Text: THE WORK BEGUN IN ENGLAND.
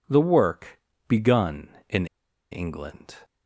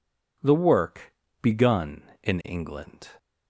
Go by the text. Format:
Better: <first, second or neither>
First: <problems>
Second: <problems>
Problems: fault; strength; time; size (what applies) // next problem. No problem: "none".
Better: second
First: pauses between "WORK" and "BEGUN"; slight; at 0.7 s; 0.30 s long // pauses between "IN" and "ENGLAND"; at 2.0 s; 0.45 s long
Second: pauses between "WORK" and "BEGUN"; slight; at 1.1 s; 0.30 s long